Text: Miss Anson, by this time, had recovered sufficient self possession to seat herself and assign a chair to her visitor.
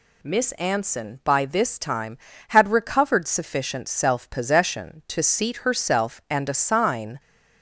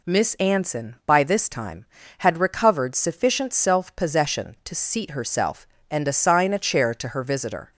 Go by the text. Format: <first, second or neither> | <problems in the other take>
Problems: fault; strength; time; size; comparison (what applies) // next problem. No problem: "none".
second | stops before "a chair to her visitor"; at 7.1 s